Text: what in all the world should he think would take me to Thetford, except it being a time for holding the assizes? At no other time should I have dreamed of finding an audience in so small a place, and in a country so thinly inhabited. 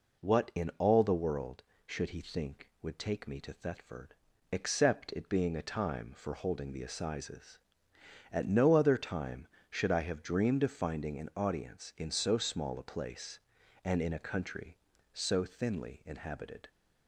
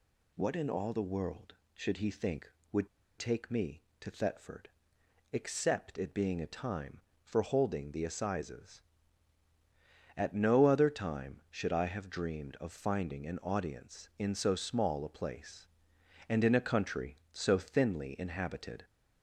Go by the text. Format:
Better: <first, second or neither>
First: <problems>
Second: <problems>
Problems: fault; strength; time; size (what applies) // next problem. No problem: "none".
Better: first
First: none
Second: pauses between "would" and "take"; slight; at 2.8 s; 0.30 s long